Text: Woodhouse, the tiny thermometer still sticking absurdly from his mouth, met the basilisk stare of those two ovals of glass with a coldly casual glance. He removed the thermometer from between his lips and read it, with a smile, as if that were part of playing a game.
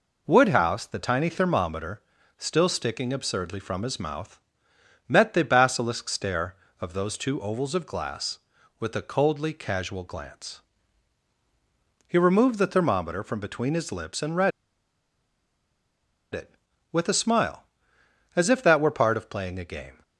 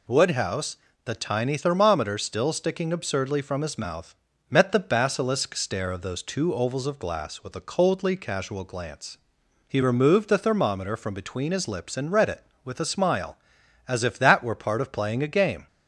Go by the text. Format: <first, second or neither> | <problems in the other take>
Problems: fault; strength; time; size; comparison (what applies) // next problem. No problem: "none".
second | pauses between "thermometer" and "still"; at 2.0 s; 0.38 s long // pauses between "read" and "it"; strong; at 14.5 s; 1.8 s long